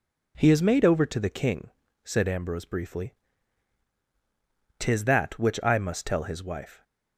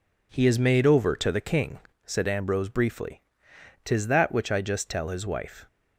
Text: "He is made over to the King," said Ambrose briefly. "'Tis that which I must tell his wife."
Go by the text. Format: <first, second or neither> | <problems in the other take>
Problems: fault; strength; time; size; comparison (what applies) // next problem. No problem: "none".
first | says "just" for "must"; at 4.6 s